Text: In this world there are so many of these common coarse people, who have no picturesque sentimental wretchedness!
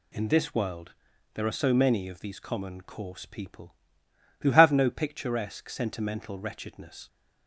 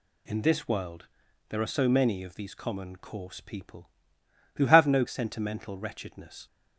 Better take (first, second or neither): first